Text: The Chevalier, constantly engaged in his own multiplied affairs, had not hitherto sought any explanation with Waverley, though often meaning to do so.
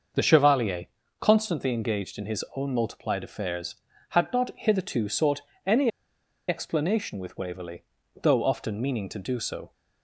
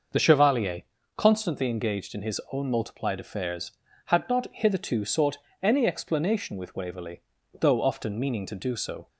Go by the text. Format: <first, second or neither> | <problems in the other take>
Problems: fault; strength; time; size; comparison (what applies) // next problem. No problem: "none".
second | starts louder than the rest; noticeable; until 1.5 s; 6 dB; noticeable in the second // pauses between "sought" and "any"; slight; at 5.3 s; 0.26 s long; slight in the second // pauses between "any" and "explanation"; noticeable; at 5.8 s; 0.58 s long